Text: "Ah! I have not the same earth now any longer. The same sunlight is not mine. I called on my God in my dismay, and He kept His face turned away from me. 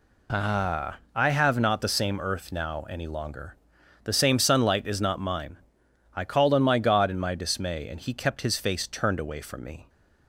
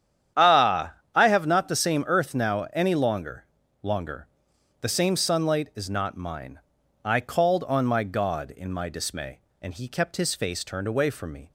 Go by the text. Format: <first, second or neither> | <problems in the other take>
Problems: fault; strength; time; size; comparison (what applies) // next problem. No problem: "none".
first | starts louder than the rest; strong; until 1.5 s; 9.5 dB // says "longer" twice; at 3.8 s